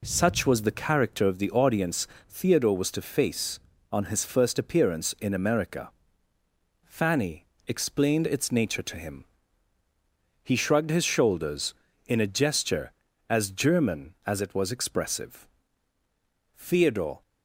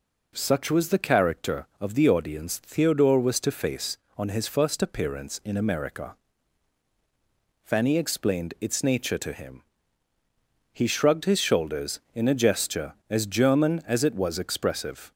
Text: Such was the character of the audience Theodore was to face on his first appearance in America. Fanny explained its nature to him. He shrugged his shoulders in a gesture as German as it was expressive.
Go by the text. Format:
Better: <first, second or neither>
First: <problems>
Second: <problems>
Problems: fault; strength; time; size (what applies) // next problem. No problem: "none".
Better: second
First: pauses between "audience" and "Theodore"; slight; at 2.0 s; 0.22 s long // pauses between "Fanny" and "explained"; slight; at 7.4 s; 0.22 s long // goes on to say "Theodore"; noticeable; from 16.5 s on; 0.66 s long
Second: none